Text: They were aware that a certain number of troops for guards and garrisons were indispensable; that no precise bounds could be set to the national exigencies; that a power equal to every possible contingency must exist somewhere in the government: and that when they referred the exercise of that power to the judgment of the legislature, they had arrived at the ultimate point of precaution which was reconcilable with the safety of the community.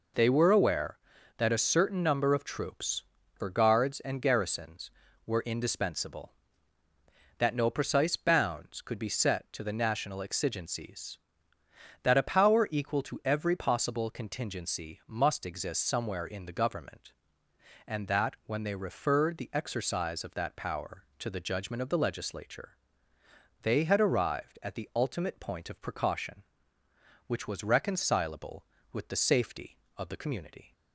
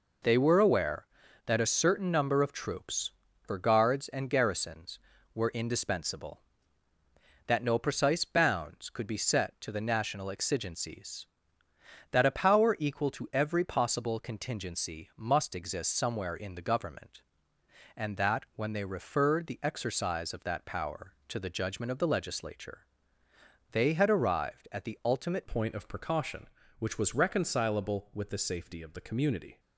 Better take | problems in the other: first | changes voice at "point"; from 25.4 s on; 4.1 s long

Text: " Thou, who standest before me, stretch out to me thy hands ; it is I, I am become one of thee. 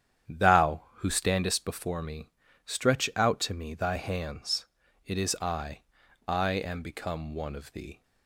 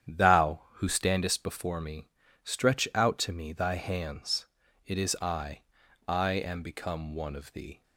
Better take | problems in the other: neither | starts louder than the rest; strong; the same in both

